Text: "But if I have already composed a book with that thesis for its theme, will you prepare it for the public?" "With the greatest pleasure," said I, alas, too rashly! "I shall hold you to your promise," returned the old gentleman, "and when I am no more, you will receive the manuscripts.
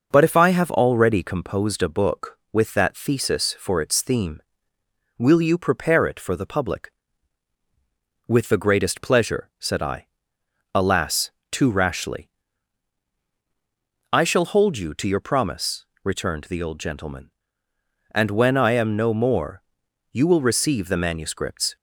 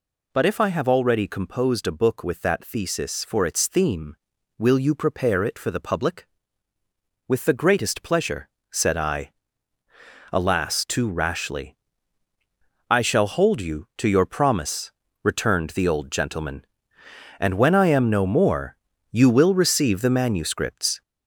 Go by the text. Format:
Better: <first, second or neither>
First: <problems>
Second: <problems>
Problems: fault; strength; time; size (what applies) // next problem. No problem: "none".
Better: first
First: none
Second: gets louder; noticeable; throughout; 5 dB